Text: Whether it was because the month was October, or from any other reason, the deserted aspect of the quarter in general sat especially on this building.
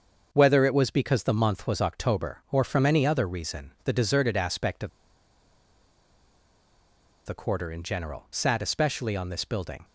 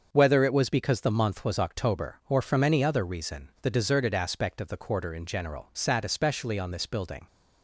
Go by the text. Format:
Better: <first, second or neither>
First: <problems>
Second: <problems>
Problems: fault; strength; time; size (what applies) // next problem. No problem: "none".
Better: second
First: starts louder than the rest; until 1.3 s; 6.5 dB // pauses between "of" and "the"; strong; at 4.9 s; 2.3 s long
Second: starts louder than the rest; until 1.1 s; 6.5 dB